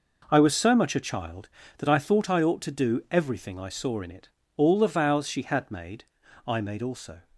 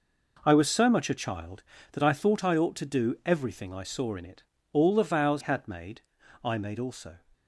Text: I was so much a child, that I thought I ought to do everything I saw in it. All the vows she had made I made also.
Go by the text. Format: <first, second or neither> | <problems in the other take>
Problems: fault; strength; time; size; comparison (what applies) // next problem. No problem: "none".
first | skips "she"; at 5.4 s // pauses between "made" and "I"; at 6.0 s; 0.42 s long; also in the first